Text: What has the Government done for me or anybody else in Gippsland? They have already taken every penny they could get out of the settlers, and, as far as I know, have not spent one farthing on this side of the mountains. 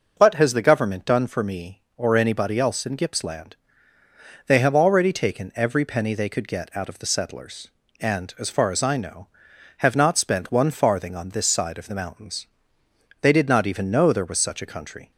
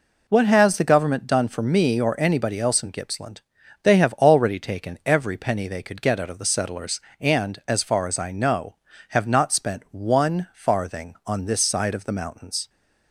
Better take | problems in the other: second | goes on to say "They did not even know there was such a country"; strong; from 13.2 s on; 1.9 s long

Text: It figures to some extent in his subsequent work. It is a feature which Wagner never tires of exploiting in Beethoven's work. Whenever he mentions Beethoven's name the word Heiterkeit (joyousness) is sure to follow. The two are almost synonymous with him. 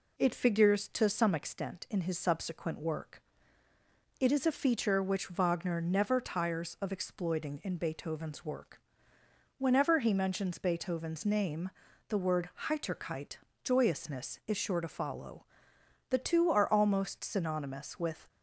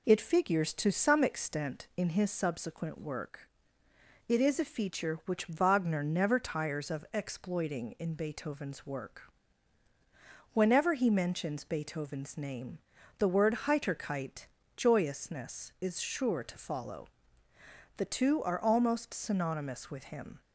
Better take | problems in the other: second | pauses between "name" and "the"; at 11.6 s; 0.40 s long; also in the second // pauses between "word" and "Heiterkeit"; slight; at 12.4 s; 0.18 s long // stops before "him"; at 18.2 s

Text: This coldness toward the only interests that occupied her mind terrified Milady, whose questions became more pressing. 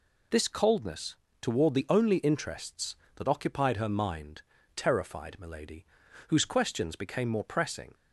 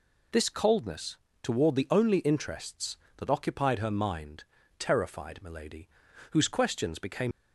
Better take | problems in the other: first | pauses between "coldness" and "toward"; slight; at 1.1 s; 0.26 s long; slight in the first // pauses between "mind" and "terrified"; slight; at 4.4 s; 0.34 s long; slight in the first // stops before "more pressing"; at 7.3 s

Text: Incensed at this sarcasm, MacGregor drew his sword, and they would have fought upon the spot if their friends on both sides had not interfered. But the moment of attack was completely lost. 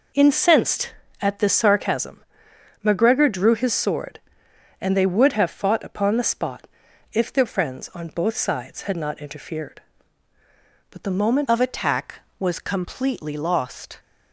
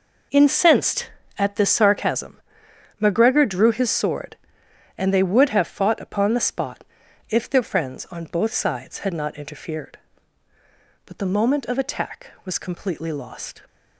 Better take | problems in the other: second | pauses between "spot" and "if"; noticeable; at 6.6 s; 0.46 s long; noticeable in the second // changes voice at "of"; from 11.4 s on; 2.5 s long

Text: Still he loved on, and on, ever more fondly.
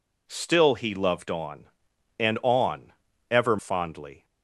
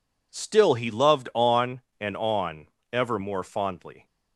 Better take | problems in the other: second | skips "more"; at 3.5 s

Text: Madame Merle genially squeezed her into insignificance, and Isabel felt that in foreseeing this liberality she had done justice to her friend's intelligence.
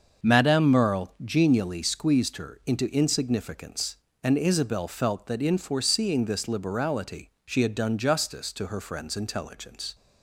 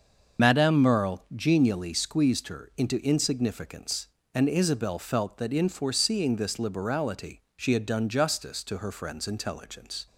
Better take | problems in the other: first | loses the start of "Madame"; at 0.3 s; 55 ms // starts louder than the rest; until 1.5 s; 6.5 dB; also in the first // pauses between "liberality" and "she"; slight; at 7.3 s; 0.16 s long; slight in the first

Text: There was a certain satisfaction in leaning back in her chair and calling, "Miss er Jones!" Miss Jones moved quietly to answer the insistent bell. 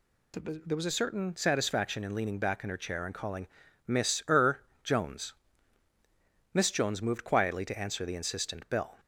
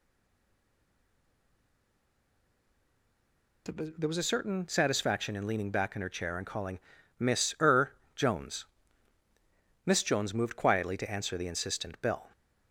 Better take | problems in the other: first | stays silent before the first word; strong; until 3.6 s; 3.6 s long // pauses between "er" and "Jones"; slight; at 7.9 s; 0.24 s long; slight in the first

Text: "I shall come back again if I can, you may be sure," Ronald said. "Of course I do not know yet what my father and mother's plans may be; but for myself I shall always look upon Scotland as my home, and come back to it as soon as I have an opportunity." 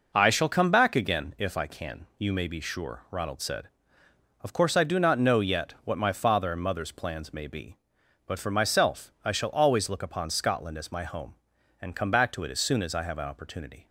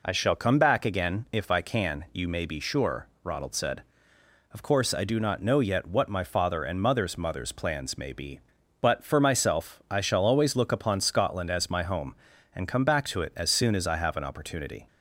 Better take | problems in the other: first | says "mother's" twice; at 7.1 s

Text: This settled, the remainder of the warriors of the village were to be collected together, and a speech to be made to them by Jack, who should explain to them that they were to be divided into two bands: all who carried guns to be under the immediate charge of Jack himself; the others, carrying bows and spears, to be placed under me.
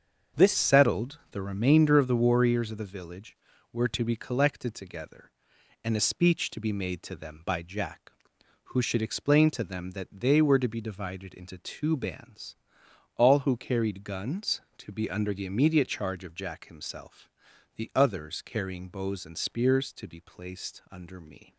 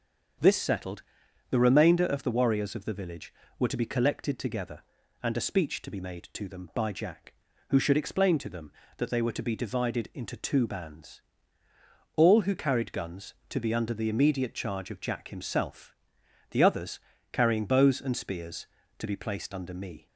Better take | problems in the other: second | starts louder than the rest; until 1.5 s; 7 dB; also in the second // changes voice at "settled"; from 0.5 s on; 21.0 s long

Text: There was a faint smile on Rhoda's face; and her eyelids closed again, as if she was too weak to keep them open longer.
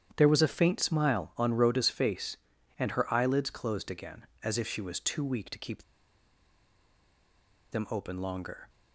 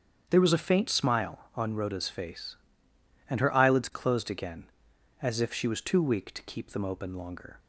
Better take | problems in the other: second | starts louder than the rest; strong; until 1.1 s; 9 dB; strong in the second // pauses between "keep" and "them"; strong; at 5.8 s; 1.8 s long

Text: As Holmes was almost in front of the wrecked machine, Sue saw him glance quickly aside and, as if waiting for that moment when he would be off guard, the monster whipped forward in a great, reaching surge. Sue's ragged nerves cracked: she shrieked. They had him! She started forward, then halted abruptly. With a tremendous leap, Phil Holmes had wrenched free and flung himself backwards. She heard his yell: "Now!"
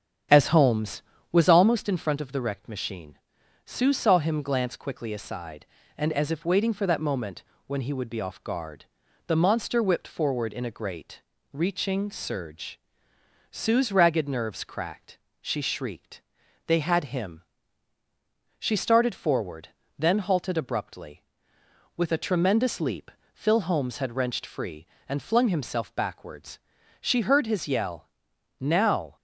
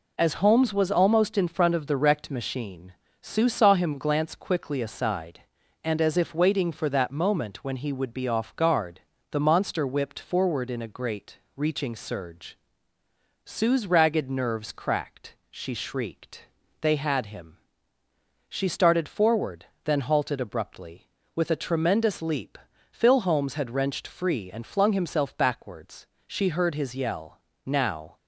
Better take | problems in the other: second | starts louder than the rest; strong; until 1.5 s; 8 dB // pauses between "moment" and "when"; slight; at 7.4 s; 0.24 s long

